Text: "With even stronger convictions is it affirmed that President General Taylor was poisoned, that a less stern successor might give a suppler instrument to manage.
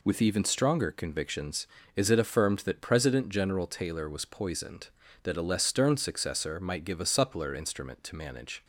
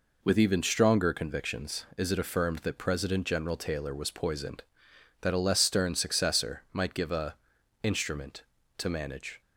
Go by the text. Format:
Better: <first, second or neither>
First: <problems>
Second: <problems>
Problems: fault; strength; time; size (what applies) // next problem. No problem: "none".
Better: first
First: none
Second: skips "suppler"; at 7.5 s